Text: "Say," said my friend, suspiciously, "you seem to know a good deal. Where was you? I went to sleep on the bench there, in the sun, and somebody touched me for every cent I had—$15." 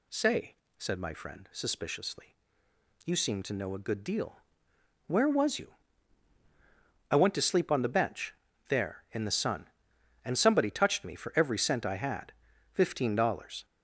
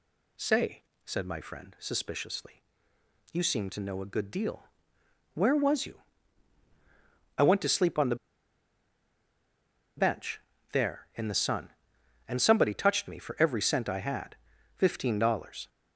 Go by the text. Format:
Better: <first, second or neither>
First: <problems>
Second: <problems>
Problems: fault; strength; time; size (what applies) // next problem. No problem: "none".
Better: first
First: pauses between "bench" and "there"; at 8.3 s; 0.36 s long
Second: pauses between "the" and "bench"; strong; at 8.1 s; 1.8 s long // pauses between "bench" and "there"; slight; at 10.3 s; 0.34 s long